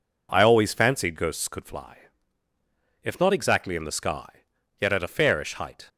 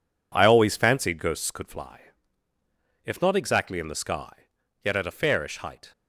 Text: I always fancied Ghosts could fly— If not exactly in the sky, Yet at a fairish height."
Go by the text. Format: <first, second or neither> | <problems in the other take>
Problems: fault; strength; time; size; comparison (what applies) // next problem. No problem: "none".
first | gets quieter; strong; throughout; 8 dB